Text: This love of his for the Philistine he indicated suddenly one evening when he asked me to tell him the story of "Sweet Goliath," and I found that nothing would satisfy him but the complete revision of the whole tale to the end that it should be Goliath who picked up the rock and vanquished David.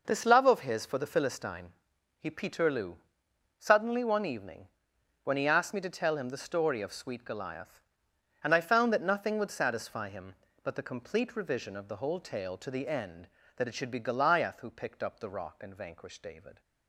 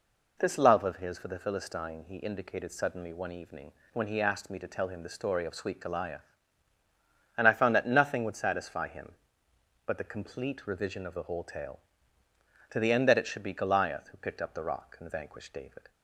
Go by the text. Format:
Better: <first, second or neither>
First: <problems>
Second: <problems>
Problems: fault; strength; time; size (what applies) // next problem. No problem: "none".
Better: second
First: pauses between "Philistine" and "he"; noticeable; at 1.7 s; 0.48 s long // says "peterloo" for "indicated"; at 2.2 s // pauses between "evening" and "when"; noticeable; at 4.6 s; 0.56 s long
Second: pauses between "evening" and "when"; slight; at 3.7 s; 0.22 s long